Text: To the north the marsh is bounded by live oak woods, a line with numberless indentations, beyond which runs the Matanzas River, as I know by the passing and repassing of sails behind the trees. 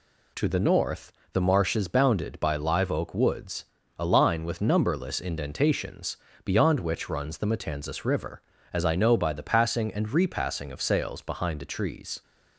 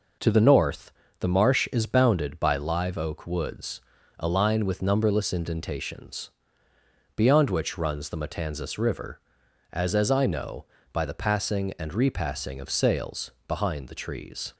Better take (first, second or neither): first